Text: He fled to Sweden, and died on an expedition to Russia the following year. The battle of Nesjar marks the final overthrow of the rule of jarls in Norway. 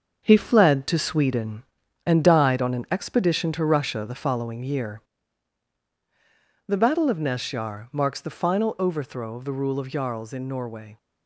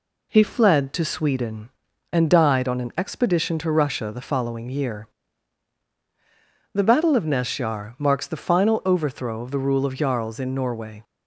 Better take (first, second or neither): second